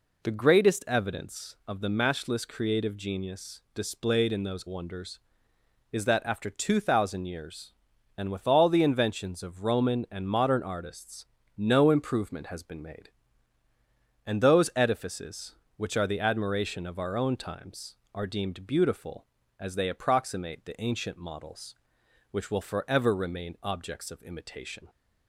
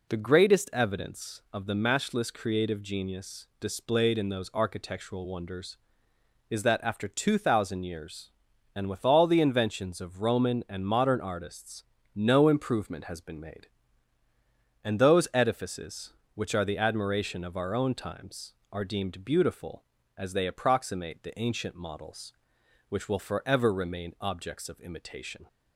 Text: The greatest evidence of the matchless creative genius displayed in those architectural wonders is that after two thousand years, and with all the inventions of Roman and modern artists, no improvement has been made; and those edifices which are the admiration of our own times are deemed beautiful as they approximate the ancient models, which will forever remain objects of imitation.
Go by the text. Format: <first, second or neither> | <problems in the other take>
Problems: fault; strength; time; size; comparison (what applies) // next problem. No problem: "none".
second | skips "architectural"; at 4.6 s